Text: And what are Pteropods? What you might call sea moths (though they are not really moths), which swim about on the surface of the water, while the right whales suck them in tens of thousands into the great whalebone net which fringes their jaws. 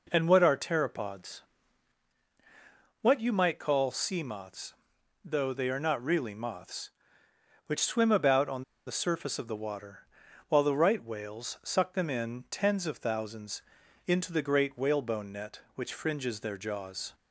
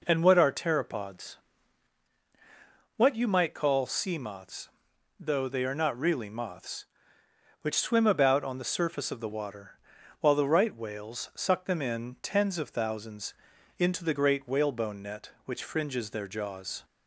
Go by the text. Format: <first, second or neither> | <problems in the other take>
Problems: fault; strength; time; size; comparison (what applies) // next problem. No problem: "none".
second | pauses between "on" and "the"; slight; at 8.6 s; 0.24 s long // pauses between "thousands" and "into"; at 13.6 s; 0.44 s long; also in the second